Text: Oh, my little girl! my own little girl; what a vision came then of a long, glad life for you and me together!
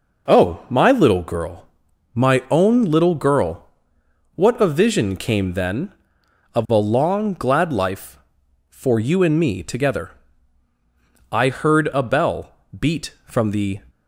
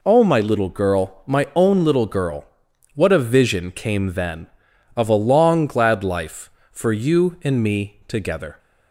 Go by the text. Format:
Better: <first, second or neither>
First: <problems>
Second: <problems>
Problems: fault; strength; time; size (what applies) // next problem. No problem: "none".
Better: second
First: goes on to say "I heard a bell beat from the"; strong; from 11.3 s on; 2.4 s long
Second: none